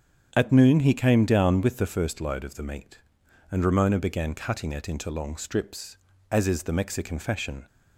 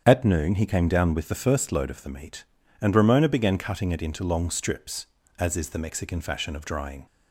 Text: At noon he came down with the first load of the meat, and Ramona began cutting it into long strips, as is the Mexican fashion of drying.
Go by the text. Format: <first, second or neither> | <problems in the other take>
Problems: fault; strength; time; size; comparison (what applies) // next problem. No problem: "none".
second | starts louder than the rest; strong; until 1.3 s; 8 dB; strong in the second // stops before "of drying"; at 7.6 s